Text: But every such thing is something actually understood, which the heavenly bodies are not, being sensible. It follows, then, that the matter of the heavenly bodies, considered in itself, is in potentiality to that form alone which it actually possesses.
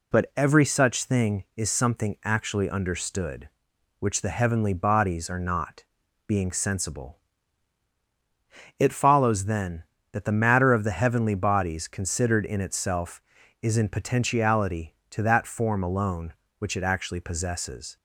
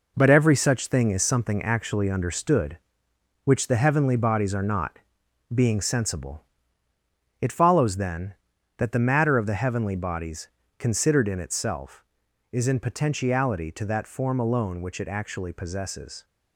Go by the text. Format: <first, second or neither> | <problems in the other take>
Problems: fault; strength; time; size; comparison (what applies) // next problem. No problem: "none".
first | gets quieter; strong; throughout; 7 dB